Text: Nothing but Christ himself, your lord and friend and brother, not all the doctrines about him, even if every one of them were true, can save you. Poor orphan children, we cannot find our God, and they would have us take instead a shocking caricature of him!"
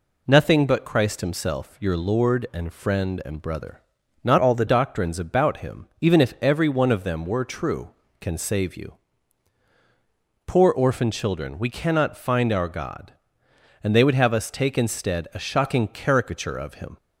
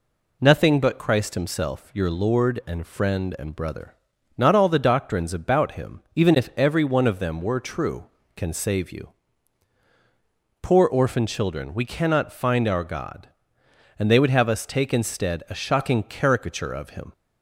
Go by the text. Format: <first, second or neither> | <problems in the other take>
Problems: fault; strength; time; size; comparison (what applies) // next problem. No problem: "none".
second | changes voice from "all" to "the"; from 4.3 to 4.6 s; 0.3 s long